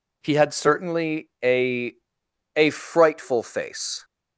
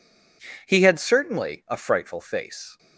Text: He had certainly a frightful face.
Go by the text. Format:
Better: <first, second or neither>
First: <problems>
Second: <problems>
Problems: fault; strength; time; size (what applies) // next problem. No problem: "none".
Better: second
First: says "a" twice; at 2.5 s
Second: none